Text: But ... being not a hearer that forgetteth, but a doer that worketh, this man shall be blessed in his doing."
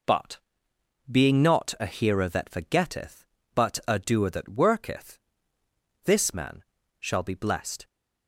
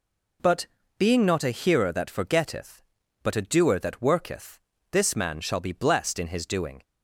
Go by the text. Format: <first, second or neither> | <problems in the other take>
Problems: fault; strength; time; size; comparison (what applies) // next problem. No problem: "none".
second | pauses between "man" and "shall"; slight; at 6.6 s; 0.36 s long // stops before "in his doing"; at 7.8 s